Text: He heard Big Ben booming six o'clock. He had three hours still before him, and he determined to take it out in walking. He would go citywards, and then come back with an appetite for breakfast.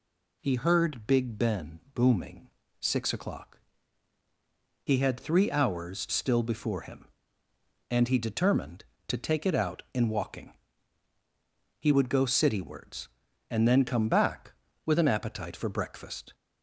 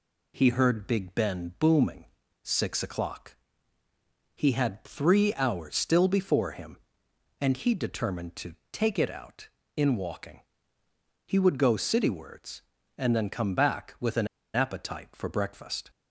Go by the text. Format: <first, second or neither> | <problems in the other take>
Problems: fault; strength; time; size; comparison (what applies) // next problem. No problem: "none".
first | pauses between "booming" and "six"; slight; at 2.0 s; 0.36 s long; slight in the first // pauses between "to" and "take"; slight; at 8.5 s; 0.18 s long // pauses between "an" and "appetite"; slight; at 14.2 s; 0.27 s long